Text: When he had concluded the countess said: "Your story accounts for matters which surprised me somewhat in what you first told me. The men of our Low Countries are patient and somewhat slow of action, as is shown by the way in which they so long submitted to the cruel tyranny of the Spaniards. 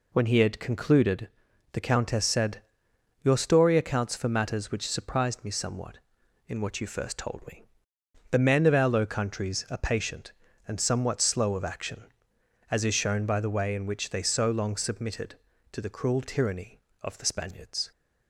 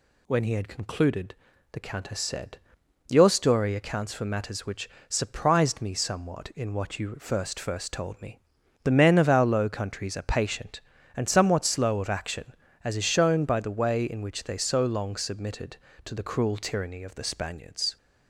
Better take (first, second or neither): first